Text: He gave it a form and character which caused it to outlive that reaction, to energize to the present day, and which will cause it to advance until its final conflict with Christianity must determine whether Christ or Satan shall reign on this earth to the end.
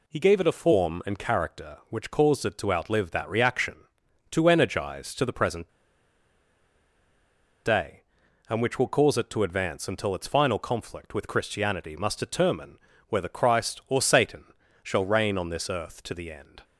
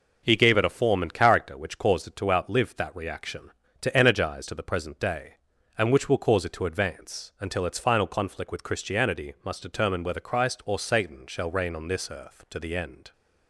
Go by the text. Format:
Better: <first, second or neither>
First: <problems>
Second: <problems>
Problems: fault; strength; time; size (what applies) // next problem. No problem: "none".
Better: second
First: pauses between "present" and "day"; strong; at 5.6 s; 1.9 s long // pauses between "determine" and "whether"; slight; at 12.7 s; 0.32 s long // pauses between "Satan" and "shall"; at 14.4 s; 0.38 s long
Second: none